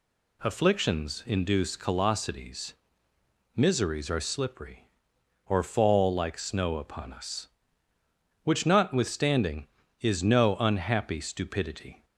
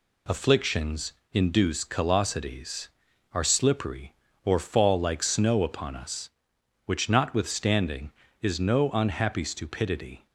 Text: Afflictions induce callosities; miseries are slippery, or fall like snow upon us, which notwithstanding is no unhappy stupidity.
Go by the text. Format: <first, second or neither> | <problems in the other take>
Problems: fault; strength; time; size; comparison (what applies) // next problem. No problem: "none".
first | pauses between "Afflictions" and "induce"; slight; at 1.1 s; 0.18 s long // skips "miseries"; at 3.1 s